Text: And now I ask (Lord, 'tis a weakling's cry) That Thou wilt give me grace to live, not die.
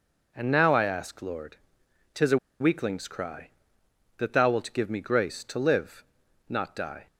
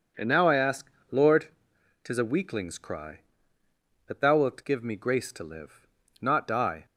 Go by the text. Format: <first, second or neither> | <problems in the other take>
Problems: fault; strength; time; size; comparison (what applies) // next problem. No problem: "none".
second | pauses between "a" and "weakling's"; slight; at 2.3 s; 0.22 s long